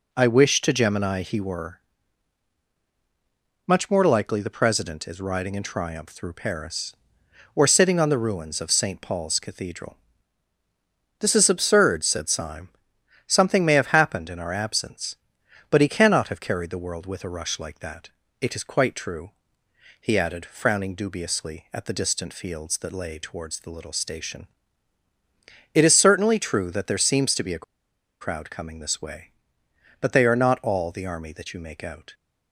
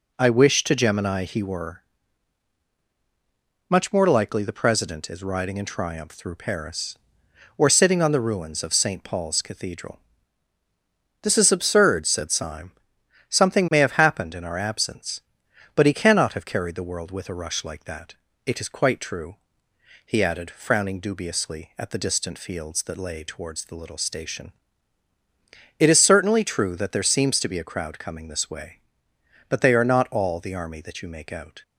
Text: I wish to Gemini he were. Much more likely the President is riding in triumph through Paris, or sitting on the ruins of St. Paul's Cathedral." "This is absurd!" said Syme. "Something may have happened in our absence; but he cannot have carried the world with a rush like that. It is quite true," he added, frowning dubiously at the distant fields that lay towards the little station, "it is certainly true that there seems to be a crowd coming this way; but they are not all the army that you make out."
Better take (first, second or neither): second